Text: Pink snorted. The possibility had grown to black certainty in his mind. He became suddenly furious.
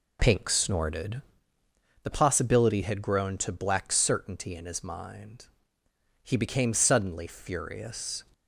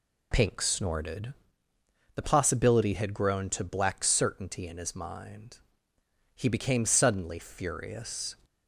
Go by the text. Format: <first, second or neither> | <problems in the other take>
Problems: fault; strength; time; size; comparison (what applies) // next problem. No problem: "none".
second | starts louder than the rest; slight; until 2.1 s; 3 dB